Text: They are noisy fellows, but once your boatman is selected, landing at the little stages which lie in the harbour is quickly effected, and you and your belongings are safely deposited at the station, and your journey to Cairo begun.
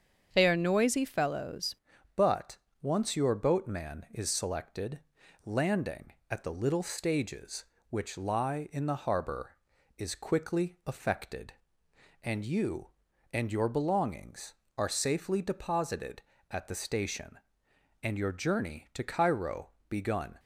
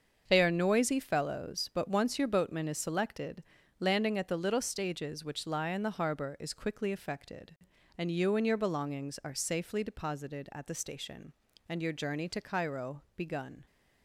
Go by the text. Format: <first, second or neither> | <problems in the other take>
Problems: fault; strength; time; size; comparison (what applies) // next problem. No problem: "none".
second | starts louder than the rest; strong; until 1.3 s; 7.5 dB; also in the second // changes voice at "but"; from 2.1 s on; 18.2 s long // pauses between "but" and "once"; slight; at 2.5 s; 0.24 s long // pauses between "Cairo" and "begun"; slight; at 19.7 s; 0.18 s long